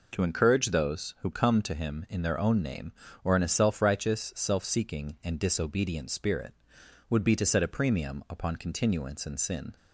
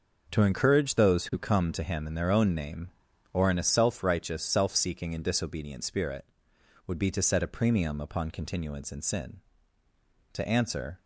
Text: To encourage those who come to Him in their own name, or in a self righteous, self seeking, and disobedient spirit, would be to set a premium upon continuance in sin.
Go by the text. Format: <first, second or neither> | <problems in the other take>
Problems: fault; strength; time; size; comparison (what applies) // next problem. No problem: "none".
first | goes on to say "To answer"; noticeable; from 10.3 s on; 0.66 s long